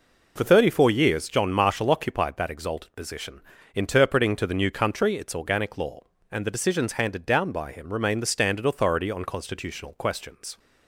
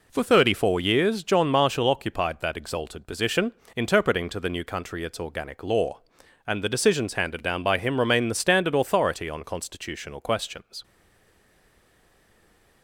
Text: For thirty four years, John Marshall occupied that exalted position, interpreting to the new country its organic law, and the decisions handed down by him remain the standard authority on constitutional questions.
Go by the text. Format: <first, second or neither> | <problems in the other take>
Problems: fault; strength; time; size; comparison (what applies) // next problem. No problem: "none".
first | stays silent after the last word; noticeable; from 10.8 s on; 2.0 s long